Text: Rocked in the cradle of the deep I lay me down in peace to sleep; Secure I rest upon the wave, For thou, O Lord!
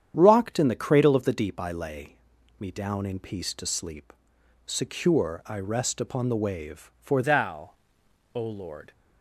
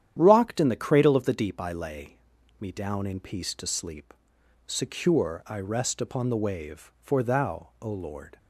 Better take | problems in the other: second | starts louder than the rest; strong; until 1.1 s; 9 dB; strong in the second // pauses between "lay" and "me"; at 2.1 s; 0.42 s long; also in the second // changes voice at "thou"; from 7.2 s on; 1.7 s long

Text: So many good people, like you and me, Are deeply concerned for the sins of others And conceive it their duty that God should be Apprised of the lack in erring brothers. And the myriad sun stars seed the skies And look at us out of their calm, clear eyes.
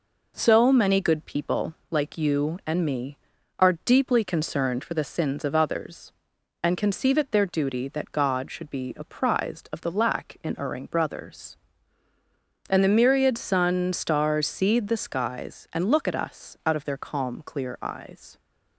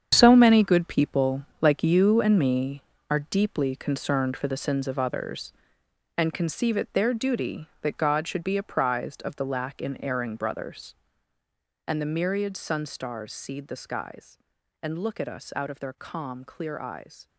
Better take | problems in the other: first | gets quieter; strong; throughout; 11 dB

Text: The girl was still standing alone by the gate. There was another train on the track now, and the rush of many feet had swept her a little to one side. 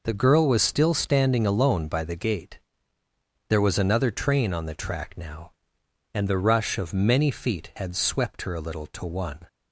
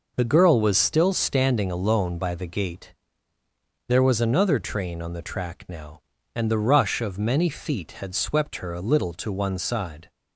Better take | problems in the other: second | stops before "side"; at 9.4 s

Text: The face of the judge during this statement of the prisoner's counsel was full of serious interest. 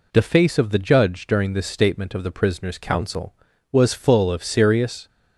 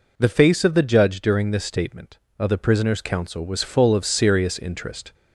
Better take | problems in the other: second | stops before "interest"; at 5.0 s

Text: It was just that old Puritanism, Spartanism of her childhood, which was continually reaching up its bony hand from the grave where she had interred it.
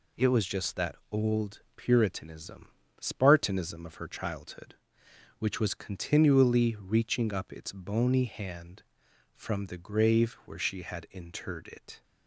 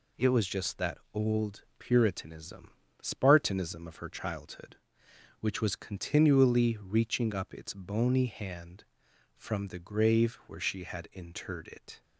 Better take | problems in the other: neither | none

